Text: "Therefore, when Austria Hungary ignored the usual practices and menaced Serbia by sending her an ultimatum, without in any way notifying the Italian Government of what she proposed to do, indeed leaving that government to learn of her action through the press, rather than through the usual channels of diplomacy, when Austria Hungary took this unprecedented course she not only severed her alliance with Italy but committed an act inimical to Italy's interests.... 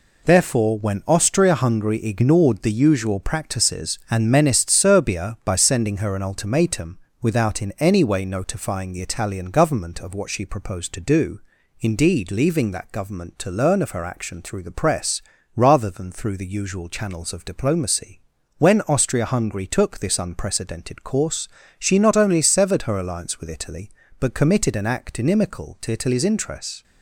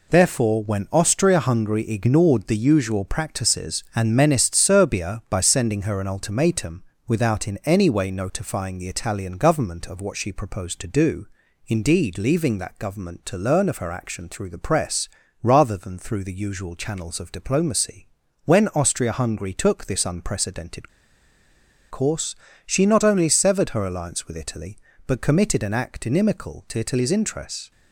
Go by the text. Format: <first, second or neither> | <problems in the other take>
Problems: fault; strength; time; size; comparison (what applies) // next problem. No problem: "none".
first | pauses between "unprecedented" and "course"; at 20.8 s; 1.0 s long // pauses between "course" and "she"; slight; at 22.3 s; 0.30 s long; slight in the first